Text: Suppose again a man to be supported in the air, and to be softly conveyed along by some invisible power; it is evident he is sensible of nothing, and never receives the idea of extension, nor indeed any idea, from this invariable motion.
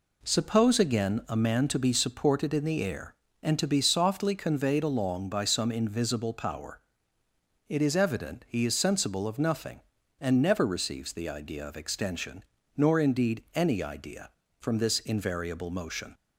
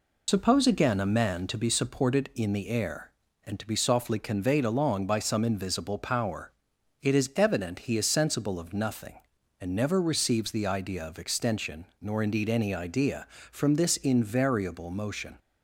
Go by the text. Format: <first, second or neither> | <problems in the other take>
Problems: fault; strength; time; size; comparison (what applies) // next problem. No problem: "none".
first | loses the start of "Suppose"; at 0.2 s; 80 ms